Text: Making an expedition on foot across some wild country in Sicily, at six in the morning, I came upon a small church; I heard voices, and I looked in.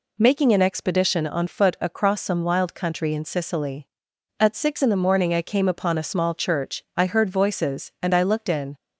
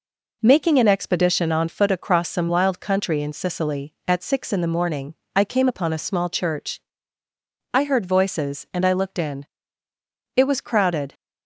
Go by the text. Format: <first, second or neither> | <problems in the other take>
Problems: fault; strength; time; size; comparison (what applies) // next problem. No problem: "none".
first | goes on to say "It was crowded"; noticeable; from 10.3 s on; 0.78 s long